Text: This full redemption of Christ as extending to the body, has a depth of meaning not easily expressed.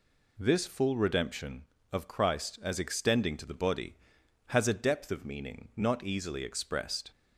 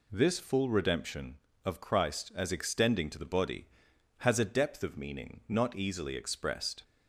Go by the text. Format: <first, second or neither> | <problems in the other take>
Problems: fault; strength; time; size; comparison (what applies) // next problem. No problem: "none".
neither | none